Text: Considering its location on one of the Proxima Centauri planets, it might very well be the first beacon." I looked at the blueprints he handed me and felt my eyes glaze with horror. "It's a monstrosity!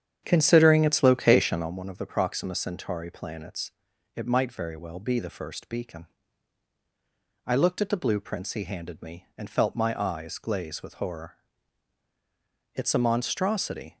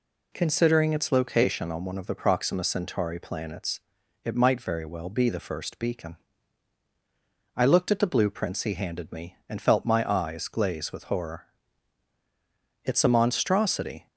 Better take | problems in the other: second | starts louder than the rest; strong; until 1.8 s; 8.5 dB

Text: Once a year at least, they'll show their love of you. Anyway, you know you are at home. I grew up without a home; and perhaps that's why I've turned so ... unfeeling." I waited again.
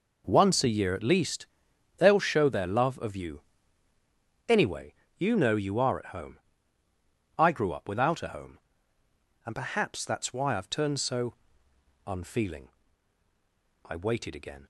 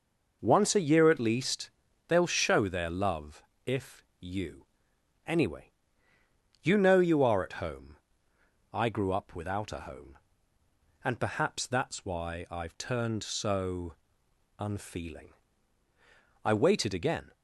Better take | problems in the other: first | says "if" for "of"; at 3.6 s

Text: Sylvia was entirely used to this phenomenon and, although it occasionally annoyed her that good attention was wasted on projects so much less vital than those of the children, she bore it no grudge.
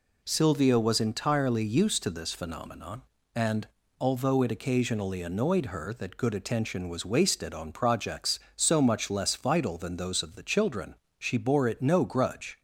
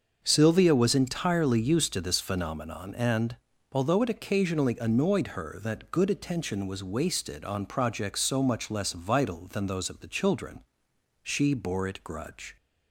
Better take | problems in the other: first | starts louder than the rest; until 1.2 s; 6.5 dB // skips "no"; at 12.0 s

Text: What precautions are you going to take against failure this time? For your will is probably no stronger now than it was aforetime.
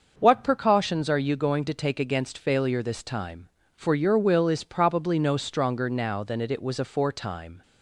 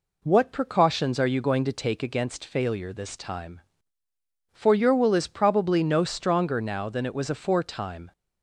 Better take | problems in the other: second | starts louder than the rest; until 1.1 s; 6.5 dB // says "it" twice; at 6.4 s

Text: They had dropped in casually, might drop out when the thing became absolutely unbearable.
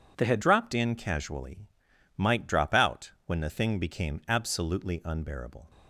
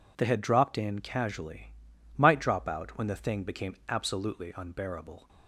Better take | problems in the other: second | changes voice at "dropped"; from 0.4 s on; 5.2 s long

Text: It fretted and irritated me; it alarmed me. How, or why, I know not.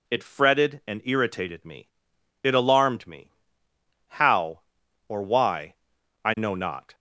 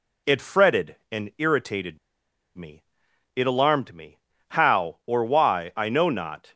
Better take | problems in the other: first | pauses between "irritated" and "me"; noticeable; at 1.9 s; 0.59 s long

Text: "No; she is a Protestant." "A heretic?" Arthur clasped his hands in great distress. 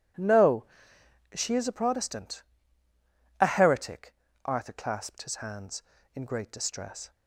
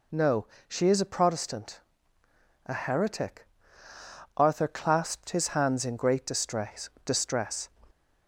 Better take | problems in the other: first | says "distress" twice; at 7.0 s

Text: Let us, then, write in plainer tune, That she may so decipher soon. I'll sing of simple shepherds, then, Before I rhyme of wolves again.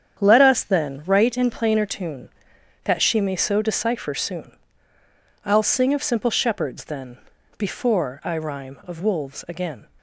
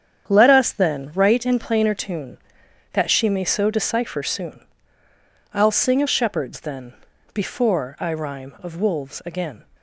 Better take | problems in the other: first | starts louder than the rest; strong; until 1.3 s; 8.5 dB; strong in the first // skips "simple"; at 6.0 s

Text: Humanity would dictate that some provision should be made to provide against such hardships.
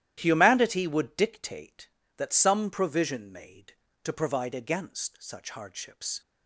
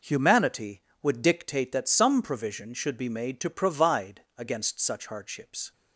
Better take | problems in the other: second | starts louder than the rest; strong; until 1.2 s; 12 dB // skips "should be"; at 3.3 s

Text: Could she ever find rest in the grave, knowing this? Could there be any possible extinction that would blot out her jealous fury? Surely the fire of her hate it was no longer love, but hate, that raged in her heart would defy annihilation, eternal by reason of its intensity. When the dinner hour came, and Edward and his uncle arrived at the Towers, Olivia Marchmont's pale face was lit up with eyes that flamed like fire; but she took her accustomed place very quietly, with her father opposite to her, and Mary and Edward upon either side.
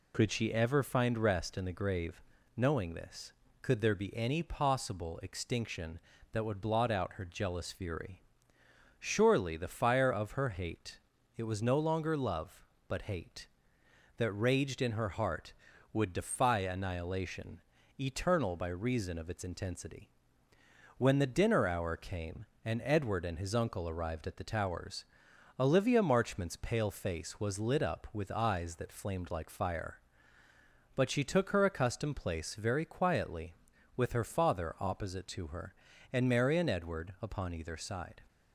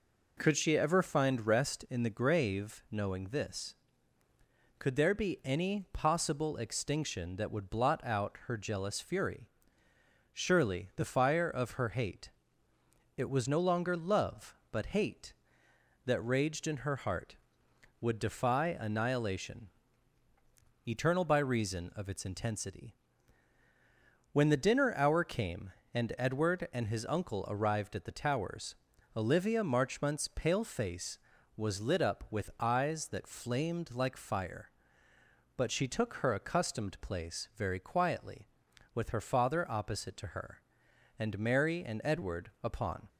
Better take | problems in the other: first | pauses between "hate" and "it"; noticeable; at 12.3 s; 0.86 s long; also in the first // stops before "either side"; at 43.0 s

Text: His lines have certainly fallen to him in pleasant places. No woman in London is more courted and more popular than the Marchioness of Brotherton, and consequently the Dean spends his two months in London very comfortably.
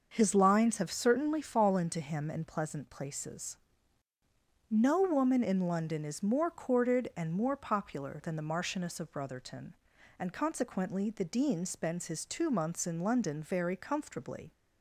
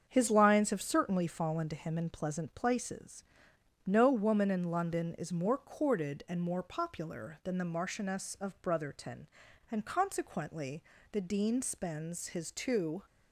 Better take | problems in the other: first | starts louder than the rest; strong; until 1.0 s; 7.5 dB; also in the first // pauses between "consequently" and "the"; slight; at 10.8 s; 0.30 s long // stops before "months in London very comfortably"; at 13.0 s

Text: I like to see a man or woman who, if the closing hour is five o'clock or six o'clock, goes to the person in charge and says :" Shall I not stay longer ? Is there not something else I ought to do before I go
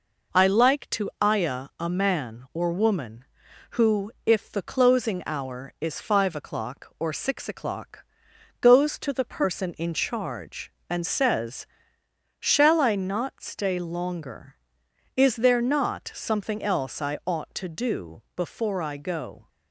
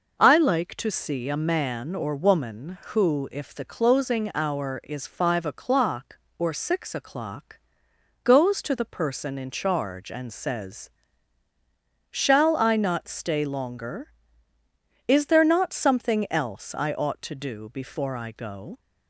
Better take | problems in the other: second | says "ayah" for "see"; at 1.2 s

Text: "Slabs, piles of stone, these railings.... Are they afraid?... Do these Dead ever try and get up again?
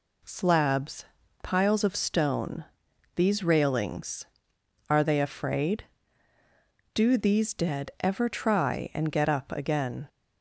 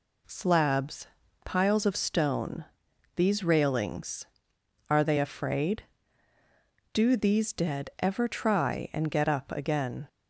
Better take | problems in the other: neither | none

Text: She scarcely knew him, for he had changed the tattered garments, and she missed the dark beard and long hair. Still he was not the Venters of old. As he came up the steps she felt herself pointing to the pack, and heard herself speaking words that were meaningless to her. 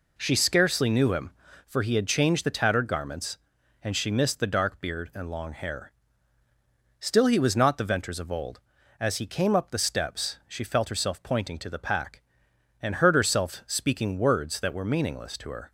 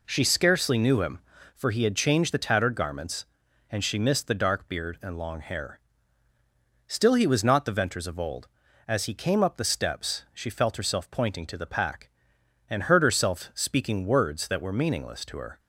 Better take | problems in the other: neither | none

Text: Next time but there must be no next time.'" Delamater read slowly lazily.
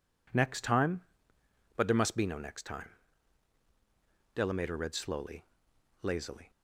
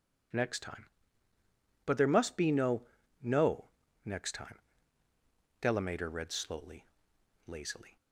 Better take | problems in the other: first | says "no" twice; at 3.2 s // pauses between "slowly" and "lazily"; noticeable; at 6.8 s; 0.62 s long; noticeable in the first

